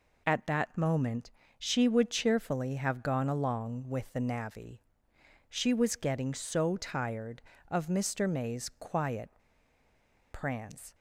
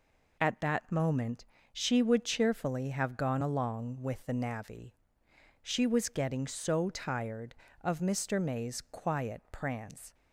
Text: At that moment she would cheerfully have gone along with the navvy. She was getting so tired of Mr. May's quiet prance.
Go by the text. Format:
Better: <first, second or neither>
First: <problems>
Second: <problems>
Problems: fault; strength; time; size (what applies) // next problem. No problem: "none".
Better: second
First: pauses between "moment" and "she"; slight; at 1.2 s; 0.28 s long // pauses between "quiet" and "prance"; at 9.2 s; 1.0 s long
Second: pauses between "moment" and "she"; slight; at 1.4 s; 0.28 s long